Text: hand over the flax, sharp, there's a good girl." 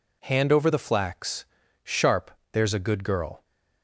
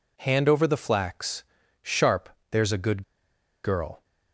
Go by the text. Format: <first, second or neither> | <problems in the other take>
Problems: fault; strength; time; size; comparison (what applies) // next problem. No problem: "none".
first | pauses between "good" and "girl"; noticeable; at 3.0 s; 0.62 s long